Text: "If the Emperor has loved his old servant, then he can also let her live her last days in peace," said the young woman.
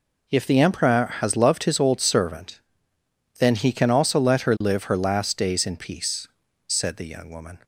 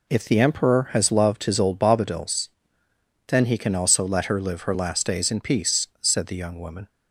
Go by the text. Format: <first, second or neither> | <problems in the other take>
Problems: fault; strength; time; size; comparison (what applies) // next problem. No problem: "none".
first | says "bobadils" for "servant"; at 1.7 s